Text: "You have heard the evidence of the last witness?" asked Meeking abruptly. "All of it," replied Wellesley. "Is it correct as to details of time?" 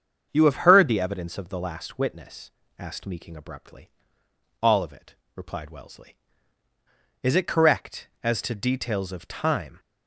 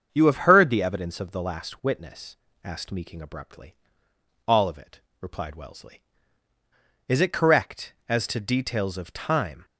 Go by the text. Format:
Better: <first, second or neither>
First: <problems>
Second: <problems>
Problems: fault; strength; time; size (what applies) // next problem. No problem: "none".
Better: neither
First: starts louder than the rest; strong; until 1.3 s; 7 dB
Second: starts louder than the rest; strong; until 1.1 s; 7 dB